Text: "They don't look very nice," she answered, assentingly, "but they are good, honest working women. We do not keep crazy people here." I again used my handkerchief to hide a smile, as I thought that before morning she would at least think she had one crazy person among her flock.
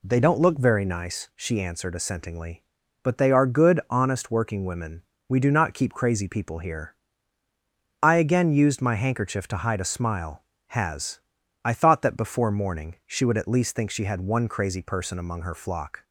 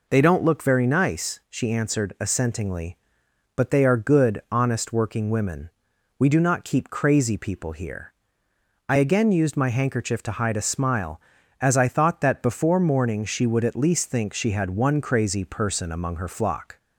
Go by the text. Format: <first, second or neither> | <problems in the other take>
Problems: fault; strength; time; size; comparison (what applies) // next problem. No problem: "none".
second | says "has" for "as"; at 10.6 s